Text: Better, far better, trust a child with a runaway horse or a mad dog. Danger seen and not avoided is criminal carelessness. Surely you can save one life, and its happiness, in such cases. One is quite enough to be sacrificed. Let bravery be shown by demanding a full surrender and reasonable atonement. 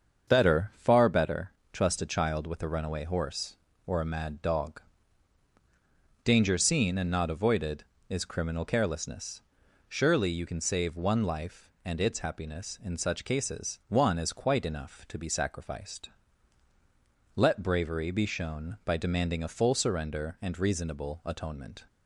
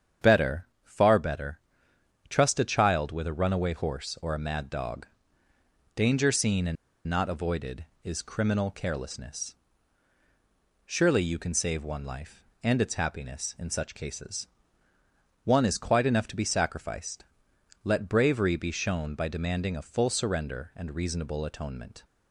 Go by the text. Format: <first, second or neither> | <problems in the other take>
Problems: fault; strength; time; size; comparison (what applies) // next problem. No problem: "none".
first | starts louder than the rest; strong; until 1.3 s; 8 dB; also in the first // pauses between "and" and "not"; slight; at 6.7 s; 0.32 s long